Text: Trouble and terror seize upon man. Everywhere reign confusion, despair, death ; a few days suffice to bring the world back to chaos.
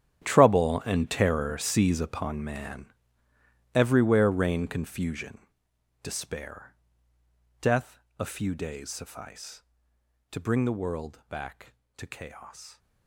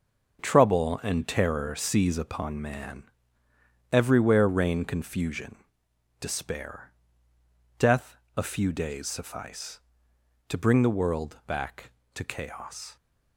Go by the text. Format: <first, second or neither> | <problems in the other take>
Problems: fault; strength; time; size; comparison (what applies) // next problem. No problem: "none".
second | gets quieter; strong; throughout; 16.5 dB // starts louder than the rest; strong; until 1.2 s; 10.5 dB; also in the second